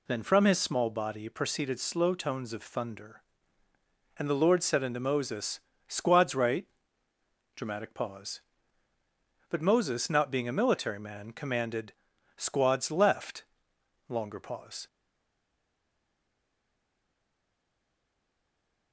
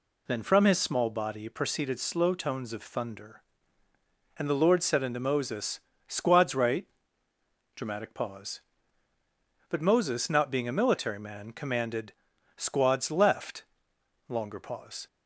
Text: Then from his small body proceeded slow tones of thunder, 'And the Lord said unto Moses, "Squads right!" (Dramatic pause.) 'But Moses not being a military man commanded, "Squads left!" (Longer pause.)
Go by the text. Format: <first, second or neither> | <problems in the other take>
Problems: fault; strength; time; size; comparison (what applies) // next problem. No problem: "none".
second | stays silent after the last word; strong; from 14.8 s on; 4.1 s long